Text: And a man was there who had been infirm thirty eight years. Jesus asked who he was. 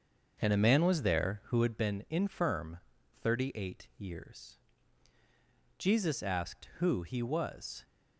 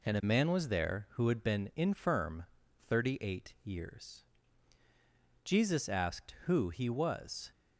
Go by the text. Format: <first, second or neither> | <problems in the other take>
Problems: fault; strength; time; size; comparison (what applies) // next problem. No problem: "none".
second | starts louder than the rest; until 1.8 s; 6.5 dB // pauses between "infirm" and "thirty"; at 2.7 s; 0.42 s long; also in the second